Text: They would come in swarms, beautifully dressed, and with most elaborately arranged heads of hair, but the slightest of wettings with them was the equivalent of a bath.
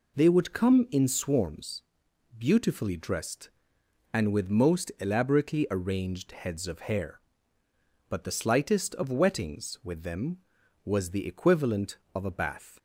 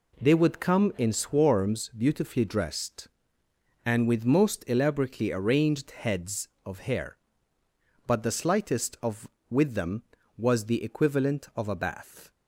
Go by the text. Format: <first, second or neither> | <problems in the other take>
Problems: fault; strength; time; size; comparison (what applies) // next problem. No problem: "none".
first | skips "wettings"; at 9.3 s